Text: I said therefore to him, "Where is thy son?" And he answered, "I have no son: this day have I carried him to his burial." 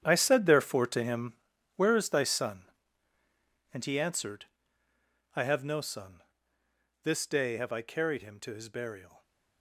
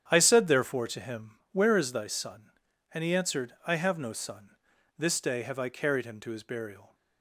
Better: second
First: gets quieter; strong; throughout; 14 dB // starts louder than the rest; strong; until 1.0 s; 9 dB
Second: starts louder than the rest; strong; until 1.0 s; 9 dB

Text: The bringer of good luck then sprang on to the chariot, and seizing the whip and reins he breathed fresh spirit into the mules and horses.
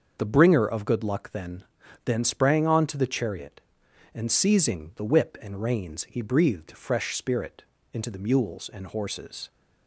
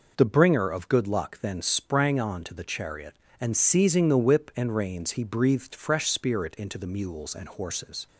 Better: second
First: starts louder than the rest; until 1.1 s; 6.5 dB // says "then" twice; at 2.0 s // pauses between "spirit" and "into"; slight; at 7.6 s; 0.28 s long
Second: none

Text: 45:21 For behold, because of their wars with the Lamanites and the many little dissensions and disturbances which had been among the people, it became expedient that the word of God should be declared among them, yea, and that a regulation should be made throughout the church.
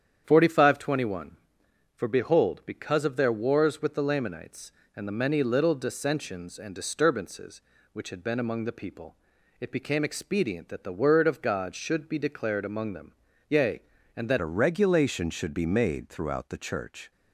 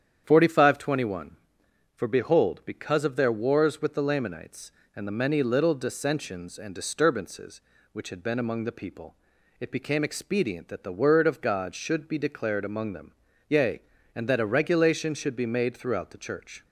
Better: second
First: starts louder than the rest; strong; until 1.2 s; 9 dB // changes voice at "a"; from 14.3 s on; 2.8 s long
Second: starts louder than the rest; strong; until 1.2 s; 9 dB

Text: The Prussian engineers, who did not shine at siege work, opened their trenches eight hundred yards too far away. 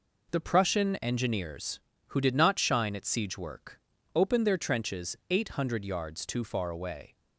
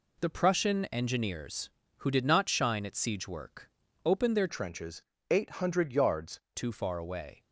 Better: first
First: none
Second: changes voice from "trenches" to "yards"; from 4.4 to 6.3 s; 1.9 s long // pauses between "trenches" and "eight"; slight; at 5.0 s; 0.26 s long

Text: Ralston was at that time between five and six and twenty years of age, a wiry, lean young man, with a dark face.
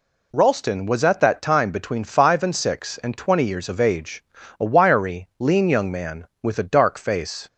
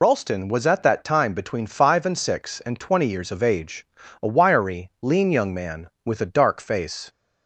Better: first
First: none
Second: loses the start of "Ralston"; at 0.0 s; 55 ms

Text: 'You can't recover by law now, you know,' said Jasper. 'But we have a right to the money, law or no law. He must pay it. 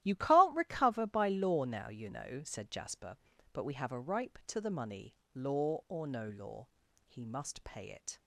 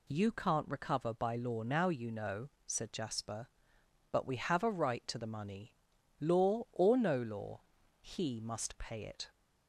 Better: second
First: starts louder than the rest; strong; until 1.0 s; 14 dB // says "ripe" for "right"; at 4.0 s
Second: none

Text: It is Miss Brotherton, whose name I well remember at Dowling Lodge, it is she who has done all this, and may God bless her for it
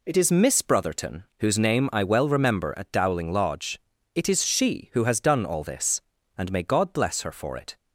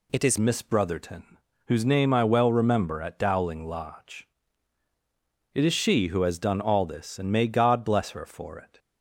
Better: first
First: none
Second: changes voice at "Miss"; from 0.3 s on; 8.4 s long

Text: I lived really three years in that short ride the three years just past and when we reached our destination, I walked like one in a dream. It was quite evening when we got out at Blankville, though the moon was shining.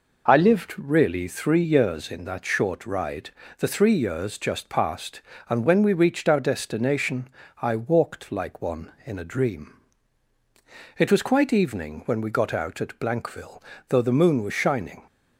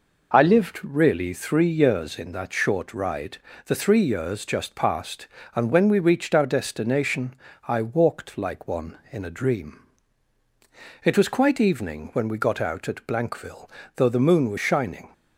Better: neither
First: pauses between "ride" and "the"; slight; at 3.2 s; 0.30 s long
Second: pauses between "ride" and "the"; slight; at 3.3 s; 0.30 s long

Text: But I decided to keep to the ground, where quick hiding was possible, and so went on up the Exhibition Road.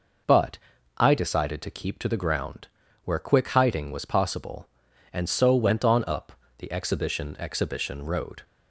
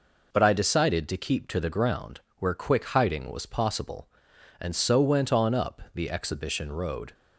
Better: second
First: pauses between "But" and "I"; at 0.5 s; 0.38 s long // pauses between "up" and "the"; slight; at 6.3 s; 0.26 s long // says "Exhibition" twice; at 7.4 s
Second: none

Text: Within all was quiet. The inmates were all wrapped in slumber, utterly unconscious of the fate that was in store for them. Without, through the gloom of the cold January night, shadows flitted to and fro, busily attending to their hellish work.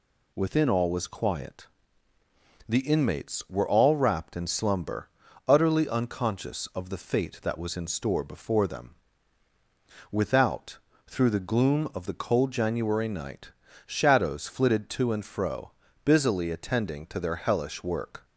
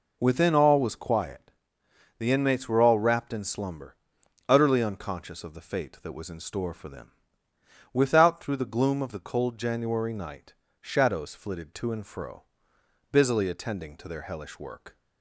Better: second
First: says "before" for "for"; at 8.2 s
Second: none

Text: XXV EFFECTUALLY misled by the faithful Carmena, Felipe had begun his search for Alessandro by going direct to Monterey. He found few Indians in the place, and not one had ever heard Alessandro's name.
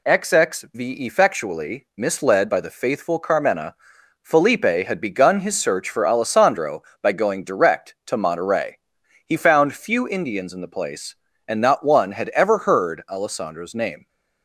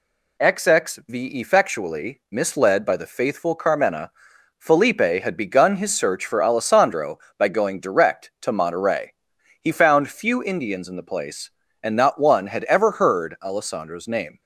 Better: neither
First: none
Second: none

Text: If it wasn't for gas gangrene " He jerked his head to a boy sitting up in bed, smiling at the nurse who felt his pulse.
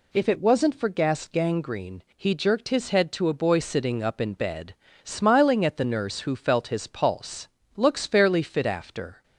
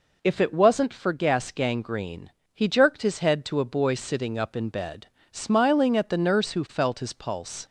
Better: second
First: goes on to say "Looks fairly fit after"; from 7.7 s on; 1.4 s long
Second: none

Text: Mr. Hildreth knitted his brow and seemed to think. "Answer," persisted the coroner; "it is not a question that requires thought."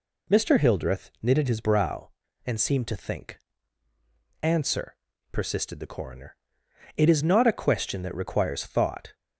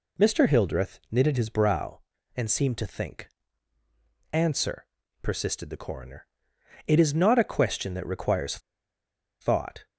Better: first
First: none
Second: pauses between "requires" and "thought"; noticeable; at 8.5 s; 0.82 s long

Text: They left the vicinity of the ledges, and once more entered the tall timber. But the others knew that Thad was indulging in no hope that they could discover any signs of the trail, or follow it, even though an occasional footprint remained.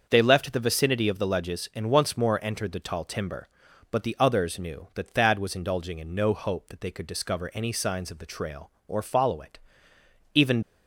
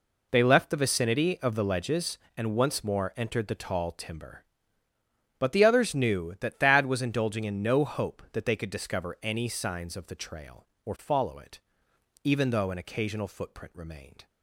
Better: second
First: starts louder than the rest; until 1.1 s; 6.5 dB // stops before "though an occasional footprint remained"; at 10.6 s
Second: none

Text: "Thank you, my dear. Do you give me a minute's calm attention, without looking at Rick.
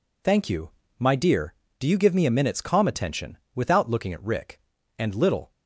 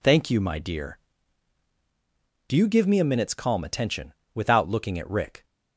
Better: second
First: goes on to say "And little"; from 4.9 s on; 0.54 s long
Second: none

